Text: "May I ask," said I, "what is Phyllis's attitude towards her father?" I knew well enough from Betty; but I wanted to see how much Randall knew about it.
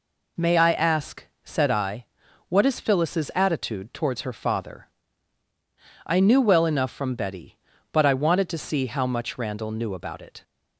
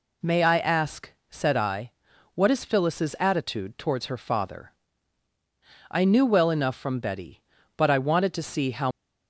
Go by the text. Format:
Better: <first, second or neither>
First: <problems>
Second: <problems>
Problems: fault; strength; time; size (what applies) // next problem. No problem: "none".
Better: first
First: none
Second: stops before "much Randall knew about it"; at 8.9 s